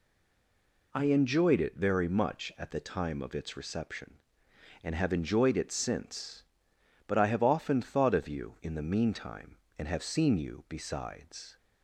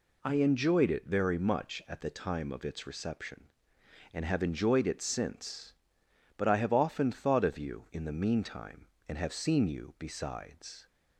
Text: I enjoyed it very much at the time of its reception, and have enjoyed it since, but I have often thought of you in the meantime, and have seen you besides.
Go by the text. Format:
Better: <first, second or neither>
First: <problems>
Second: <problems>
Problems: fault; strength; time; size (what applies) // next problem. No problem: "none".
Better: second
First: stays silent before the first word; slight; until 0.9 s; 0.9 s long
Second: none